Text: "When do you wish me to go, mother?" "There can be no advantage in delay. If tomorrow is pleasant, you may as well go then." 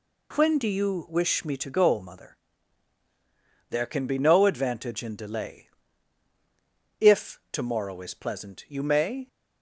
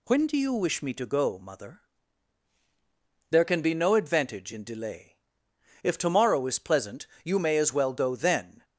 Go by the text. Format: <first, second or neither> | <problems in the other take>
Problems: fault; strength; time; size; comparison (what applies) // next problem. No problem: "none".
second | stops before "as well go then"; at 9.2 s